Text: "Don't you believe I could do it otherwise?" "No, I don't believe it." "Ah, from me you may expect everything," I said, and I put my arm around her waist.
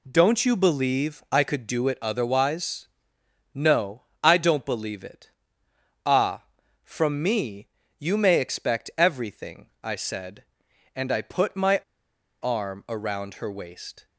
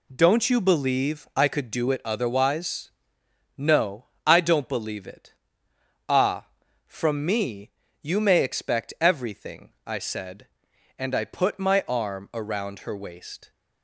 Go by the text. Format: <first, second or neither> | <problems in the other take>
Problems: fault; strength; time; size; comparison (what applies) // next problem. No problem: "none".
second | pauses between "me" and "you"; slight; at 7.6 s; 0.32 s long; slight in the second // pauses between "my" and "arm"; noticeable; at 11.7 s; 0.64 s long